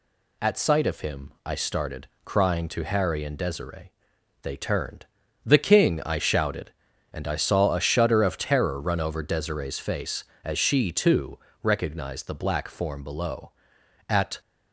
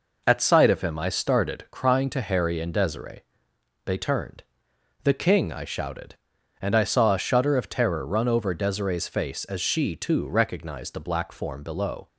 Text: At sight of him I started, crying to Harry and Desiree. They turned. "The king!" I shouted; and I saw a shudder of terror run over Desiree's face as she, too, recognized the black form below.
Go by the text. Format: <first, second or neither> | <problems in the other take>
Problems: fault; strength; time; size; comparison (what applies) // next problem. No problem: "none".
second | goes on to say "At"; slight; from 14.1 s on; 0.30 s long